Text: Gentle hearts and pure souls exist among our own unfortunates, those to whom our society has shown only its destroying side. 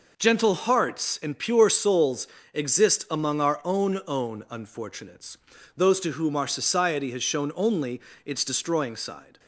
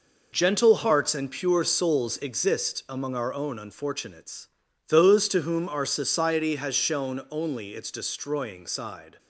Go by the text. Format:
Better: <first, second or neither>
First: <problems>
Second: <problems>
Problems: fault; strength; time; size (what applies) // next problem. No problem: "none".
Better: second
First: pauses between "souls" and "exist"; slight; at 2.2 s; 0.26 s long // says "own" twice; at 4.0 s // pauses between "only" and "its"; slight; at 8.0 s; 0.24 s long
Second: none